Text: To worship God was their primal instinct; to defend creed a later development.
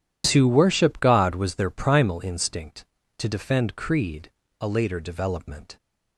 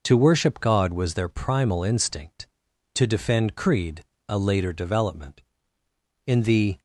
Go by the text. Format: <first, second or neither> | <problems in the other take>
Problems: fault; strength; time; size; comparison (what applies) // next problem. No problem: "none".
first | pauses between "creed" and "a"; slight; at 4.0 s; 0.28 s long; slight in the first // goes on to say "In the"; from 6.2 s on; 0.54 s long